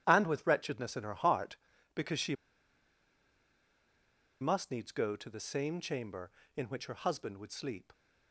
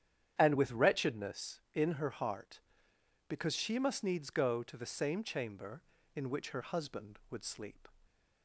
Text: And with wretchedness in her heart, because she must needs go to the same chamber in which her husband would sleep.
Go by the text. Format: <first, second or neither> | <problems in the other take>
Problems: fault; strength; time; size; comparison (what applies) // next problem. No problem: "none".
second | starts louder than the rest; strong; until 1.0 s; 10.5 dB; strong in the second // pauses between "she" and "must"; strong; at 2.3 s; 2.0 s long